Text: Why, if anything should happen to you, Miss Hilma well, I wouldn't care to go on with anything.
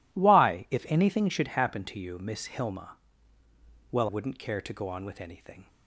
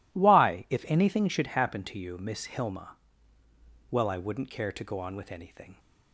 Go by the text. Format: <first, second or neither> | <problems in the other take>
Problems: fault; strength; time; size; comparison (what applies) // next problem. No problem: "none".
second | pauses between "Hilma" and "well"; noticeable; at 2.9 s; 0.96 s long; noticeable in the second // skips "I"; at 4.0 s